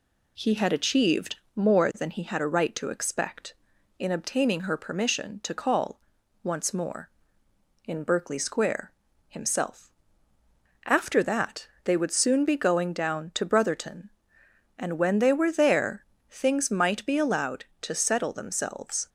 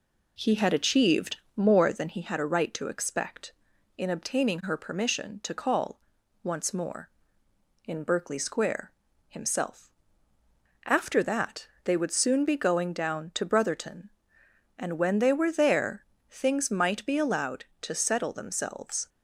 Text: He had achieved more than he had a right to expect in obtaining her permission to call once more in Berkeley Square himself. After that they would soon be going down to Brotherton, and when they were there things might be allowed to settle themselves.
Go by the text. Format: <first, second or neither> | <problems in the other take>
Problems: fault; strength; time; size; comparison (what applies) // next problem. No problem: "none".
first | starts louder than the rest; slight; until 2.1 s; 3.5 dB // pauses between "achieved" and "more"; slight; at 1.3 s; 0.18 s long; slight in the first // pauses between "call" and "once"; noticeable; at 5.9 s; 0.46 s long; noticeable in the first // pauses between "Square" and "himself"; slight; at 8.9 s; 0.34 s long; slight in the first // pauses between "that" and "they"; slight; at 11.6 s; 0.16 s long; slight in the first // pauses between "there" and "things"; slight; at 16.0 s; 0.26 s long; slight in the first